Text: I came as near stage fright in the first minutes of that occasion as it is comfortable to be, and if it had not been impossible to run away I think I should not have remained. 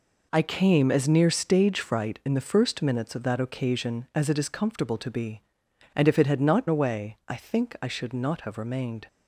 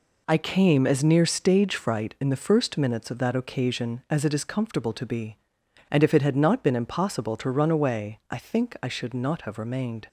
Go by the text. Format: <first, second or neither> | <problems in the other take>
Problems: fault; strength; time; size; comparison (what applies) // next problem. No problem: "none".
second | skips "been impossible to run"; at 6.6 s